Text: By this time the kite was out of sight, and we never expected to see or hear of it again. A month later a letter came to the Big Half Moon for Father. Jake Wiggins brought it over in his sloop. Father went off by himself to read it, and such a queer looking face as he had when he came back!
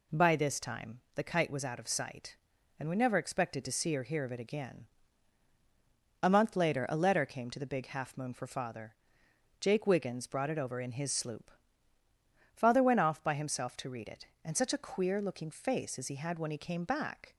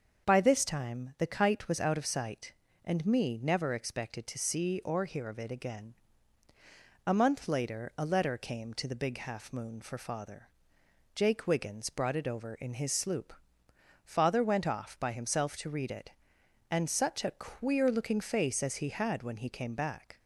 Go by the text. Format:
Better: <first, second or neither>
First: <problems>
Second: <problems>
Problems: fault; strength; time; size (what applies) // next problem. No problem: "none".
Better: first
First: none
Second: starts louder than the rest; until 1.3 s; 6.5 dB // says "me" for "we"; at 3.0 s